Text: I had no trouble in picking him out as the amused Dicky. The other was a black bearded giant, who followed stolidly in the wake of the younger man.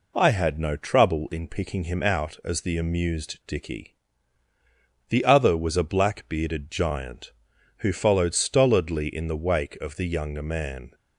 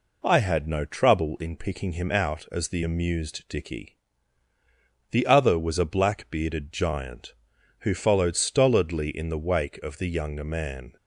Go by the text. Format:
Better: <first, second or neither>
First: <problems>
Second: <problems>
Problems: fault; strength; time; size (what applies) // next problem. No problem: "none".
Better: neither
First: none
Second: none